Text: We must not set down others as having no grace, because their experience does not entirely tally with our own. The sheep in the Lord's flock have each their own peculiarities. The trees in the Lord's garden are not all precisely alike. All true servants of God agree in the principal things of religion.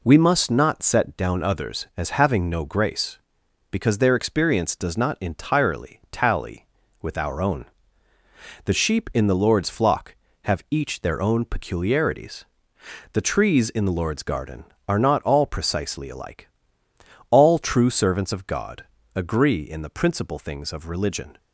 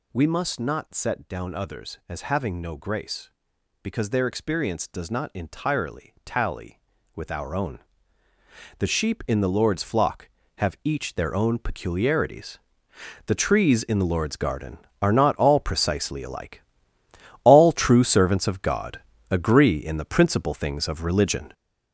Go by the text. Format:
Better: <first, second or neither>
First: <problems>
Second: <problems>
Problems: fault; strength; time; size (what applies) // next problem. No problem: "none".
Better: first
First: pauses between "God" and "agree"; slight; at 18.8 s; 0.32 s long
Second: gets louder; strong; throughout; 7.5 dB // pauses between "God" and "agree"; slight; at 18.9 s; 0.32 s long